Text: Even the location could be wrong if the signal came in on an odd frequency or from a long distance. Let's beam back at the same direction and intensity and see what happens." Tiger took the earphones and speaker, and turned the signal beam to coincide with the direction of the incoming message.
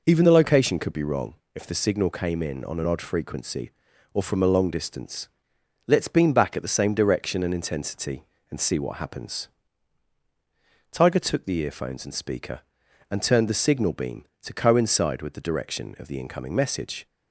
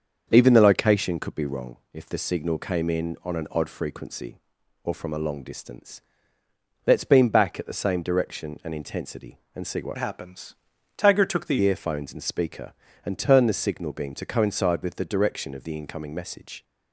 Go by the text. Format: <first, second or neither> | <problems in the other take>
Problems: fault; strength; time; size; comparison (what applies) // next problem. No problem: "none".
first | starts louder than the rest; until 1.3 s; 6.5 dB // pauses between "wrong" and "if"; slight; at 1.7 s; 0.16 s long; slight in the first // changes voice from "happens" to "the"; from 9.9 to 11.5 s; 1.6 s long